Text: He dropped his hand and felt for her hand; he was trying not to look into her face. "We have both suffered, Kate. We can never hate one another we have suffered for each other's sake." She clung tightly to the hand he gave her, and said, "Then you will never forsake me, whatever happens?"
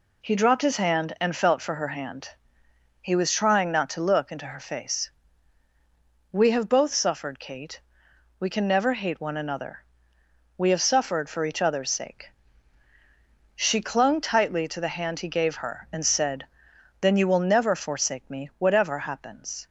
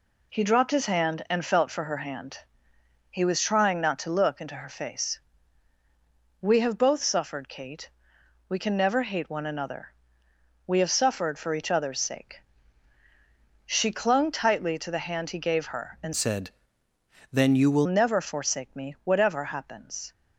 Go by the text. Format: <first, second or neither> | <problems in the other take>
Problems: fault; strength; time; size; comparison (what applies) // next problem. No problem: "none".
first | pauses between "another" and "we"; noticeable; at 9.9 s; 0.76 s long; noticeable in the first // changes voice from "said" to "will"; from 16.1 to 17.8 s; 1.7 s long